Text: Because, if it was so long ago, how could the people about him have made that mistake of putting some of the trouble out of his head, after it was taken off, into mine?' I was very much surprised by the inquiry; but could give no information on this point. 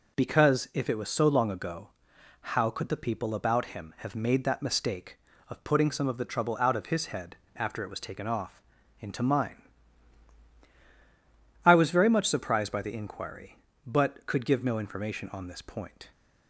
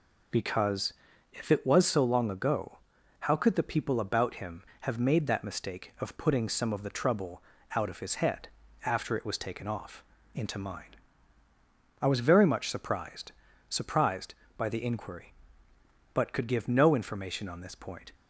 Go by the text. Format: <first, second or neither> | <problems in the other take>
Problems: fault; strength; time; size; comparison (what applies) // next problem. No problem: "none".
first | pauses between "trouble" and "out"; slight; at 7.4 s; 0.32 s long // says "surprised" twice; at 13.6 s